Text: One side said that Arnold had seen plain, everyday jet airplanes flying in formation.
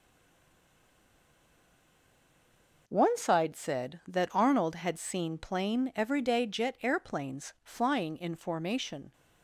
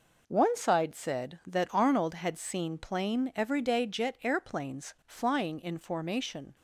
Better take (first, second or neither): second